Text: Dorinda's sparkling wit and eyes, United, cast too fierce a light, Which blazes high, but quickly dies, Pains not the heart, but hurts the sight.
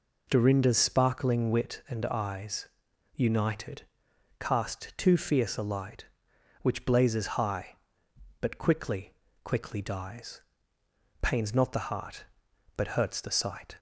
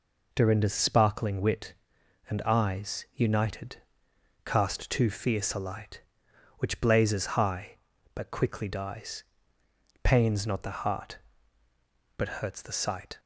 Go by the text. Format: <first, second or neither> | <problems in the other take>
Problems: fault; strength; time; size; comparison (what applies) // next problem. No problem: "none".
second | says "quickly" twice; at 9.4 s